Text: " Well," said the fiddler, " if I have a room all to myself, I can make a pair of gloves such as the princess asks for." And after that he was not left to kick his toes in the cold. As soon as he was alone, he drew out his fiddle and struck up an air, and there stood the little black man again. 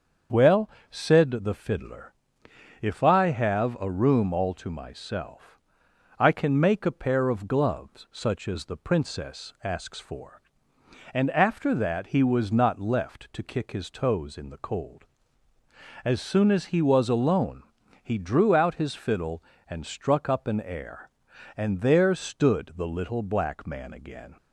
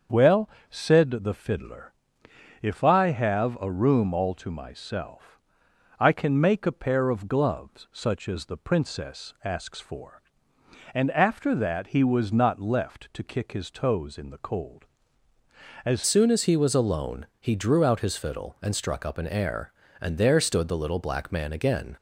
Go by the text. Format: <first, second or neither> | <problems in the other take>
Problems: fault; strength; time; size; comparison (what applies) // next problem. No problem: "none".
first | starts louder than the rest; until 1.3 s; 6.5 dB; also in the first // changes voice at "soon"; from 16.0 s on; 5.9 s long